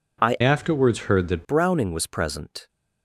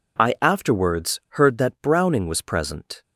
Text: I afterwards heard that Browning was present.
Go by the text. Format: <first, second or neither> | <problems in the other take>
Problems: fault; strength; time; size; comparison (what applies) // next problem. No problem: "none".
second | changes voice from "afterwards" to "that"; from 0.4 to 1.4 s; 1.0 s long